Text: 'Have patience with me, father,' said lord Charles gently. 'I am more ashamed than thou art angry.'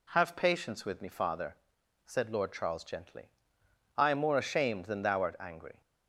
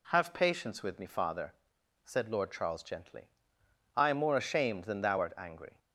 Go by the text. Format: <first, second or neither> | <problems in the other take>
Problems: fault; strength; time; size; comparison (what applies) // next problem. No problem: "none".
neither | none